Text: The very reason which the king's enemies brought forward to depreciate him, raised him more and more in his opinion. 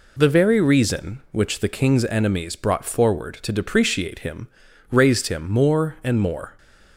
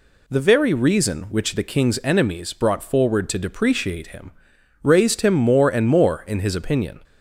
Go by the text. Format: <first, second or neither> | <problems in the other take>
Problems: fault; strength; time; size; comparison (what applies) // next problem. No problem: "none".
second | stops before "in his opinion"; at 6.5 s